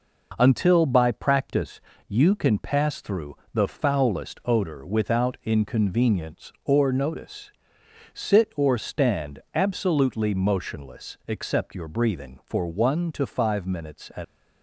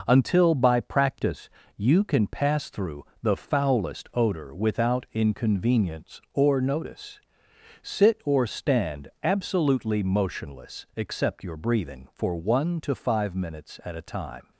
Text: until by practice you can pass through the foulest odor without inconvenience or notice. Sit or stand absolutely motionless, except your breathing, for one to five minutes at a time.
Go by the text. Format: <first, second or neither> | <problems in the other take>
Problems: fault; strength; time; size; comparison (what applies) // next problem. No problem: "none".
second | pauses between "practice" and "you"; slight; at 1.8 s; 0.28 s long; slight in the second // pauses between "through" and "the"; slight; at 3.3 s; 0.18 s long; slight in the second // stops before "a time"; at 14.2 s